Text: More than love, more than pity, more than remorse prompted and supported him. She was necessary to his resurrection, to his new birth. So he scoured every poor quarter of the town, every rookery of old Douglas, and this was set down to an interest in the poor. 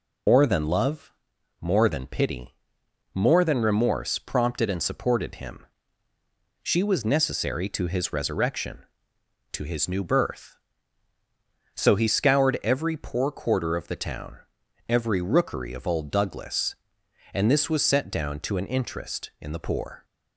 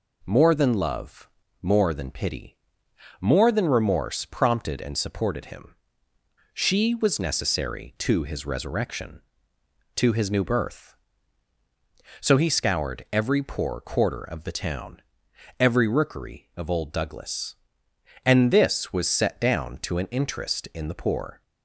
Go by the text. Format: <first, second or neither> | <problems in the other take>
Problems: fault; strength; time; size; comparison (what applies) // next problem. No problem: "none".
second | loses the start of "More"; at 0.2 s; 135 ms